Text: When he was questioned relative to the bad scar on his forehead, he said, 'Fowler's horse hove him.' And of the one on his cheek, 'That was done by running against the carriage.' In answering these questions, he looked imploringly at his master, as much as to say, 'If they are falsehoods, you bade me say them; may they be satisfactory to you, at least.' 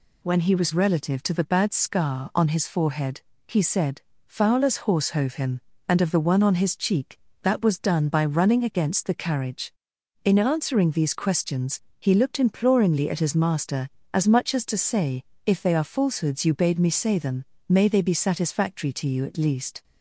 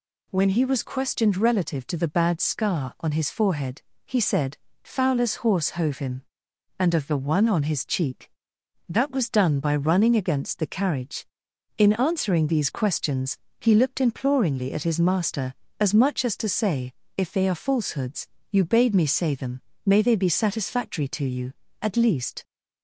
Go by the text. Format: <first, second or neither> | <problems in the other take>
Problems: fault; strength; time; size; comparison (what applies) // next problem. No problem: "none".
second | skips "questioned"; at 0.7 s